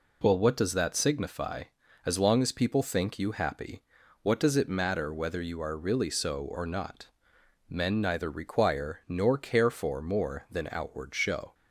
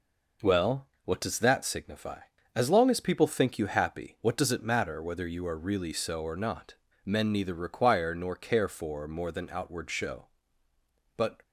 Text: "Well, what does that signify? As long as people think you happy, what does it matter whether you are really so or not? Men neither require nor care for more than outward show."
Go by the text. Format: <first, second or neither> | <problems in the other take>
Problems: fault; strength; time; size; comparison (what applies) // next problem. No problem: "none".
first | goes on to say "But"; slight; from 11.1 s on; 0.26 s long